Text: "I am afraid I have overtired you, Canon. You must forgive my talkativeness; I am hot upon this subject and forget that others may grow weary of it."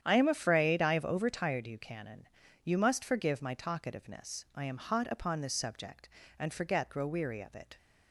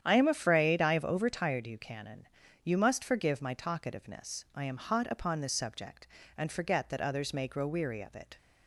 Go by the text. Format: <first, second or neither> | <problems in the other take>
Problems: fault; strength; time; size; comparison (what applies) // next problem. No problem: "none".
second | starts louder than the rest; strong; until 1.0 s; 9.5 dB; strong in the second // skips "that others may"; at 6.9 s